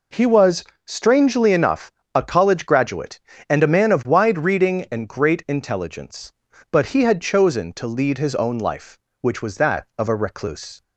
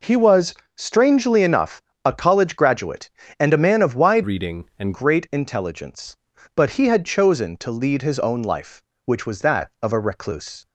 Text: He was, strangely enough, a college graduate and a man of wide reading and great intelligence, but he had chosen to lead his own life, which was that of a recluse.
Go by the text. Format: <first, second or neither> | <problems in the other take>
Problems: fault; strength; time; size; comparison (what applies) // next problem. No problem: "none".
first | changes voice from "reading" to "and"; from 4.2 to 4.9 s; 0.7 s long